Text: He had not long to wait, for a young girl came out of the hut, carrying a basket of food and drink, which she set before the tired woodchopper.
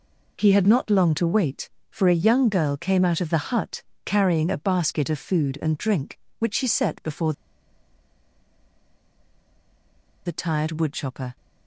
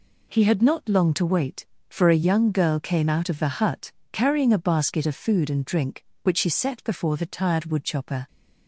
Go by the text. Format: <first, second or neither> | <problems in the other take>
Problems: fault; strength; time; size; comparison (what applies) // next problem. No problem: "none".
second | pauses between "before" and "the"; strong; at 7.3 s; 2.9 s long